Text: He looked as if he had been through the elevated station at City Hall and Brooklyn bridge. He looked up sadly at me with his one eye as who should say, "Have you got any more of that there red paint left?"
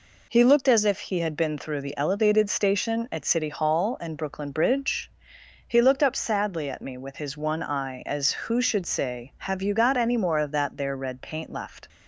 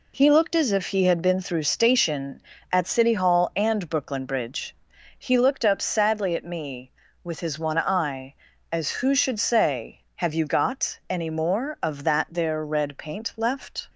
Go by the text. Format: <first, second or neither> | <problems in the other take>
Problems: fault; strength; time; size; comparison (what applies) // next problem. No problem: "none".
first | skips "the elevated"; at 1.6 s